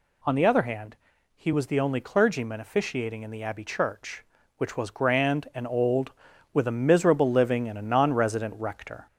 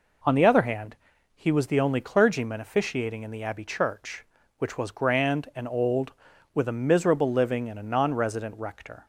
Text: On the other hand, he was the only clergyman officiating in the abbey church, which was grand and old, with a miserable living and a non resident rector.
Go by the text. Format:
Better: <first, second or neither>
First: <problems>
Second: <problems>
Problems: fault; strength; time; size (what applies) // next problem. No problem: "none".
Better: second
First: gets louder; slight; throughout; 2.5 dB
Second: none